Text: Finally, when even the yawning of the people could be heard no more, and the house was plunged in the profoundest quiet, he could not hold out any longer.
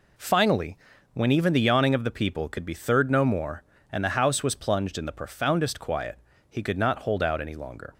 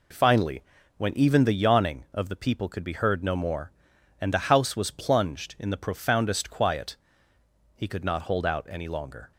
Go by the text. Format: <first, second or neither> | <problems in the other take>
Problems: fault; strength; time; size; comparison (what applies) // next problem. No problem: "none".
second | says "third" for "heard"; at 2.7 s